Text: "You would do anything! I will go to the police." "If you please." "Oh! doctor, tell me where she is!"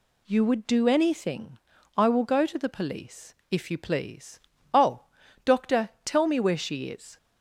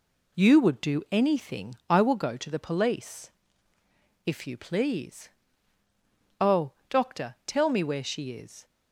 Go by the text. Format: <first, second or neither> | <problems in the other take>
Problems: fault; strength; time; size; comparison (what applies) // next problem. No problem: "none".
neither | none